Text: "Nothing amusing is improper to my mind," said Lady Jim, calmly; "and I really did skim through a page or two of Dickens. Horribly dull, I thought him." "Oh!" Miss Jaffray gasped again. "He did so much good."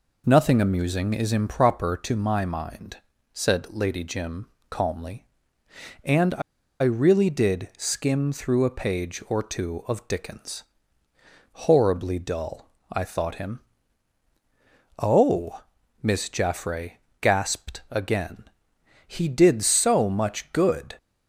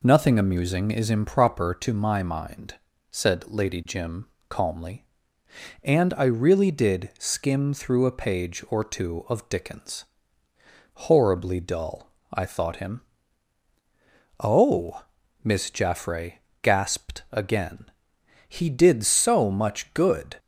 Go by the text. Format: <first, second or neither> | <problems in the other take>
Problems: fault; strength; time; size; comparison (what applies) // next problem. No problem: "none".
second | pauses between "I" and "really"; at 6.4 s; 0.41 s long // pauses between "Jaffray" and "gasped"; slight; at 16.9 s; 0.26 s long; slight in the second